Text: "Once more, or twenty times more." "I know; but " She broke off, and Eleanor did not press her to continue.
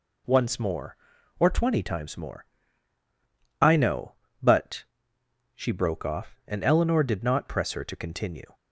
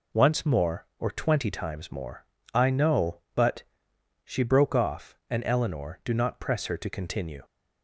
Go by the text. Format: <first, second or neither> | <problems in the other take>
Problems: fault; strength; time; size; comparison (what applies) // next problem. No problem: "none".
first | says "do" for "did"; at 6.0 s